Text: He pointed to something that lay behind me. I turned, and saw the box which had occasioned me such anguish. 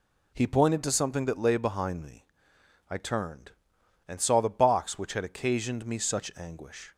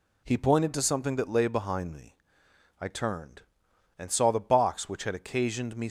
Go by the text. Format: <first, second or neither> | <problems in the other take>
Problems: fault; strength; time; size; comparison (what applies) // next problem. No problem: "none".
first | stops before "such anguish"; at 5.8 s